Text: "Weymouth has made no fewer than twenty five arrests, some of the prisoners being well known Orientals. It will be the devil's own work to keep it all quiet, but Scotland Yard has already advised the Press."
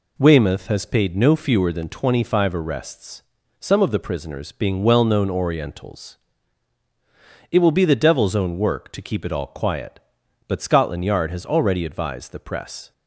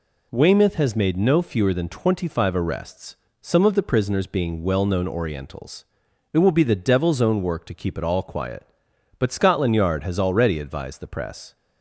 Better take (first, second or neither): second